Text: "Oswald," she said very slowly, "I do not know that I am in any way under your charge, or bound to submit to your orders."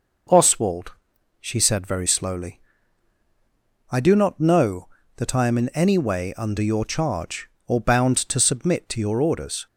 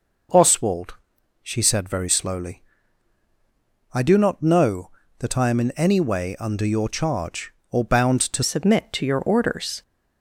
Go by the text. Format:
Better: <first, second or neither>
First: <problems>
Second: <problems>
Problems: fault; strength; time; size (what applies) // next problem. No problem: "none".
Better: first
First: none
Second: changes voice at "submit"; from 8.4 s on; 1.4 s long